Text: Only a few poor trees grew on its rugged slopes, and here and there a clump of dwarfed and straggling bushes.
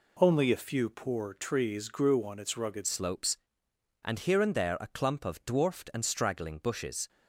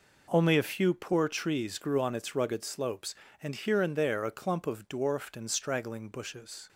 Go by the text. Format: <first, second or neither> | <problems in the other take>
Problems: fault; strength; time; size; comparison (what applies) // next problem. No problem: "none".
second | changes voice at "slopes"; from 2.8 s on; 4.2 s long